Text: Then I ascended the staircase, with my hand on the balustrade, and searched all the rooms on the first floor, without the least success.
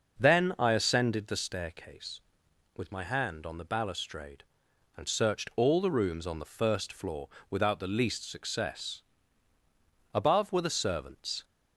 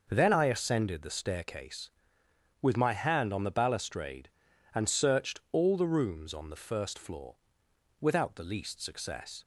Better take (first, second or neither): second